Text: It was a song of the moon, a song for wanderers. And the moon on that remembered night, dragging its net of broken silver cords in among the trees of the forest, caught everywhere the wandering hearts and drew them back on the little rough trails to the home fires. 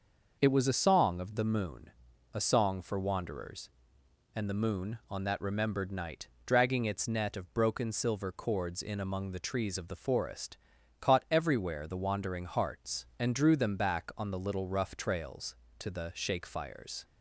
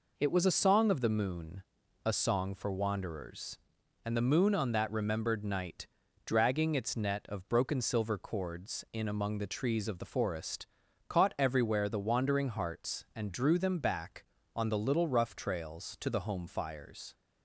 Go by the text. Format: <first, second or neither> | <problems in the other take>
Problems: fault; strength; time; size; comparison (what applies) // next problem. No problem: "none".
second | starts louder than the rest; noticeable; until 1.4 s; 6 dB // says "shake" for "home"; at 16.1 s